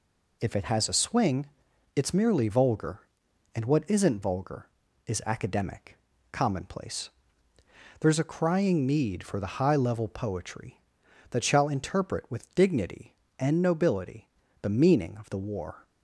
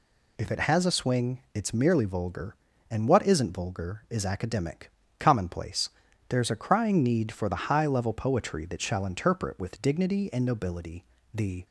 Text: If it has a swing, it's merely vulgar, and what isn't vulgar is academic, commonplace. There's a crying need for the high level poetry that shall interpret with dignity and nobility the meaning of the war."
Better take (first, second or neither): first